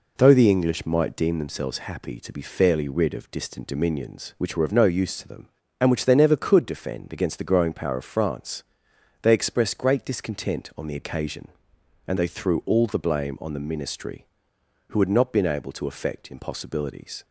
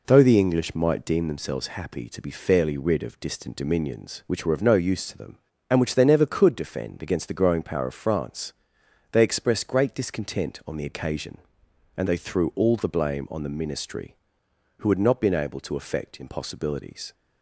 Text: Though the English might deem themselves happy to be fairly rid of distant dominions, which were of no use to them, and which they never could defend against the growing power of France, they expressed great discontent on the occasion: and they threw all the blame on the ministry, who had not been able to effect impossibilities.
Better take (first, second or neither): neither